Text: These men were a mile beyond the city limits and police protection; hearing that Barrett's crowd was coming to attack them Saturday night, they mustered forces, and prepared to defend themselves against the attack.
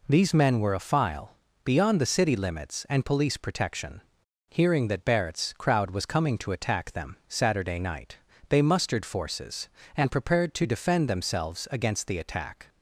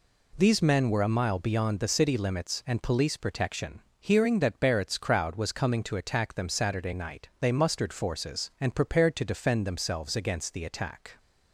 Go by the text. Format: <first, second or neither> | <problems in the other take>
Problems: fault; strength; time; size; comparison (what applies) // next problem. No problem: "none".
second | says "file" for "mile"; at 0.7 s